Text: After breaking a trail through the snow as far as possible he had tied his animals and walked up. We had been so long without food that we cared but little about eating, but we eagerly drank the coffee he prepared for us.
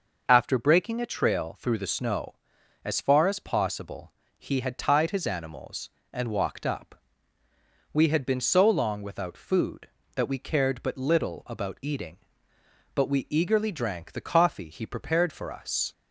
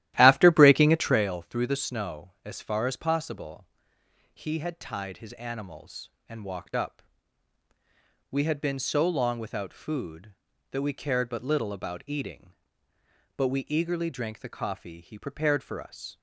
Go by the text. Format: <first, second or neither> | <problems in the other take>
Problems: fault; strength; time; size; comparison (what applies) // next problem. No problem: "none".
first | starts louder than the rest; strong; until 1.3 s; 14 dB // pauses between "possible" and "he"; noticeable; at 3.6 s; 0.66 s long; slight in the first